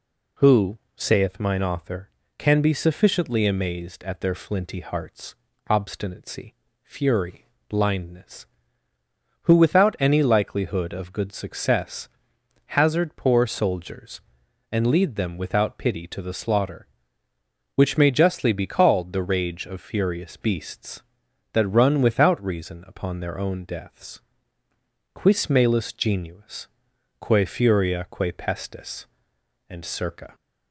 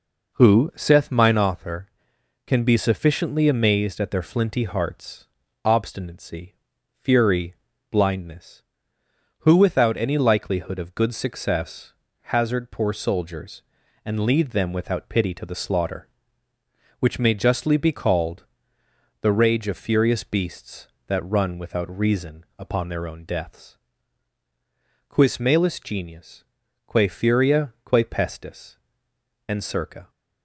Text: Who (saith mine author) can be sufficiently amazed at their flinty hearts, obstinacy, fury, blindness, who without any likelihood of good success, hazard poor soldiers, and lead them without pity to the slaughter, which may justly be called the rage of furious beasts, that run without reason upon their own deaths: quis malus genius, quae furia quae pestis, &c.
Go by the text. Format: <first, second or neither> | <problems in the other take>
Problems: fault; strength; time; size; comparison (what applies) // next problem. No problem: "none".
first | starts louder than the rest; noticeable; until 1.6 s; 4.5 dB // pauses between "called" and "the"; noticeable; at 18.4 s; 0.74 s long